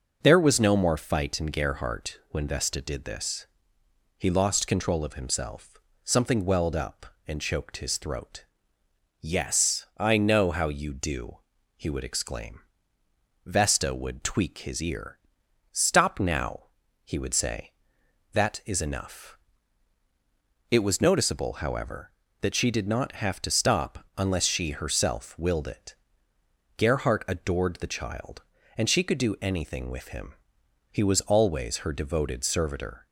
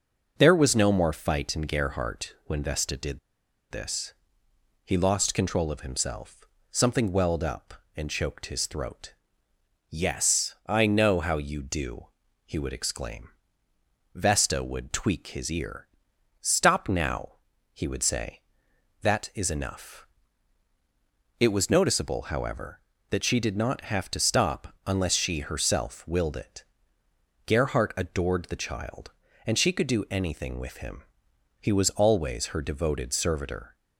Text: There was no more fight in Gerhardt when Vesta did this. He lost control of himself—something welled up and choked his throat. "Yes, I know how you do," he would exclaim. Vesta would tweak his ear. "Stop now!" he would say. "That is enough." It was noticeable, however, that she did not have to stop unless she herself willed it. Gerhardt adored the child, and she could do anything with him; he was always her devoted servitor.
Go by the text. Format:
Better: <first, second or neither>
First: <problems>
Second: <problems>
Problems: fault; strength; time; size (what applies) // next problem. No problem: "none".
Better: first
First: none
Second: pauses between "did" and "this"; noticeable; at 3.1 s; 0.52 s long